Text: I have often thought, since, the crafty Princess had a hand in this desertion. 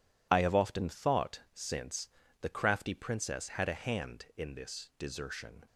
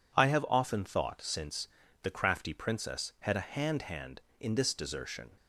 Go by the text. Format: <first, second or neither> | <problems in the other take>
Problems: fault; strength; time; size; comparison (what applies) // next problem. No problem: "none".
first | says "hand" twice; at 3.8 s